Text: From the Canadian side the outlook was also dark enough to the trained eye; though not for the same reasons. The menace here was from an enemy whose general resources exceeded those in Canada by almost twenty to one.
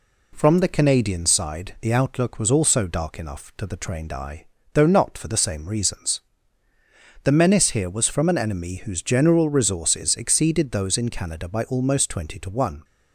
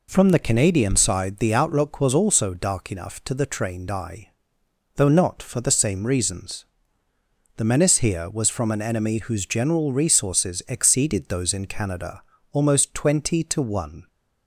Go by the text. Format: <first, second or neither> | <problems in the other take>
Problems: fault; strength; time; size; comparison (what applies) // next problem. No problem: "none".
first | skips "by"; at 12.3 s